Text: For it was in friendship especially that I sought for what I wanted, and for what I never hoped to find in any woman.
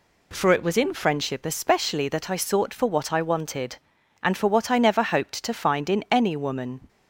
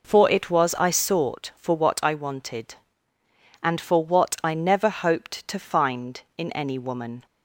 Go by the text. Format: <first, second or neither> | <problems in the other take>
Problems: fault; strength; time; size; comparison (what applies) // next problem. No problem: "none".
first | skips "in friendship especially that"; at 0.7 s